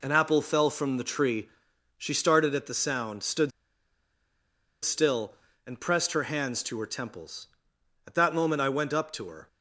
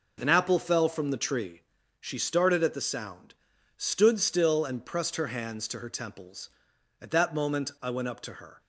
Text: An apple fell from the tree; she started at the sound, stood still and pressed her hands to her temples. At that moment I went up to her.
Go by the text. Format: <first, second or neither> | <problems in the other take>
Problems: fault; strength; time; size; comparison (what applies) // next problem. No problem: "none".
second | pauses between "stood" and "still"; strong; at 3.5 s; 1.3 s long